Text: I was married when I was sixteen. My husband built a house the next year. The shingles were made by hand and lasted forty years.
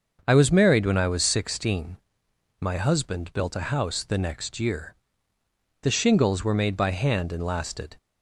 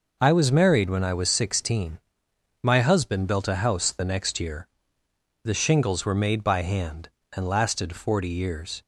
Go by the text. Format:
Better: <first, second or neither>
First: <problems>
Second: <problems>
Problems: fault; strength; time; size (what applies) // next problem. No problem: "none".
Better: second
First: starts louder than the rest; until 1.2 s; 6.5 dB // stops before "forty years"; at 7.9 s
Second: none